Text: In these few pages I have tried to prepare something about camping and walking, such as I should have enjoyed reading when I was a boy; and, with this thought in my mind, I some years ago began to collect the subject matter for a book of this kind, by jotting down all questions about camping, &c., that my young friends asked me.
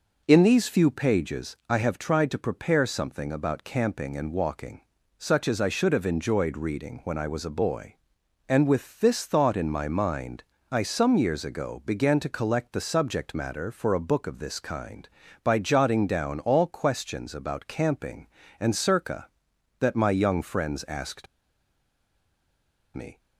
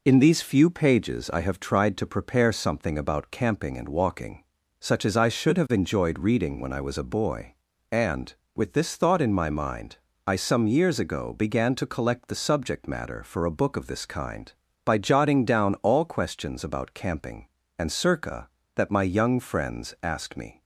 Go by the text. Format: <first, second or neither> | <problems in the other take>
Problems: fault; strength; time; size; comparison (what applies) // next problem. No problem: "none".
second | pauses between "asked" and "me"; strong; at 21.2 s; 1.6 s long